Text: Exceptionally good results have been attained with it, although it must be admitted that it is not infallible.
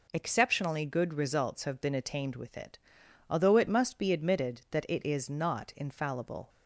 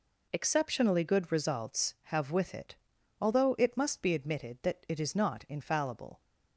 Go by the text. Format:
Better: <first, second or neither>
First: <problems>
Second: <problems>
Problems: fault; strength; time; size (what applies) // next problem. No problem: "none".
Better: first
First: none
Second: skips "been attained"; at 2.3 s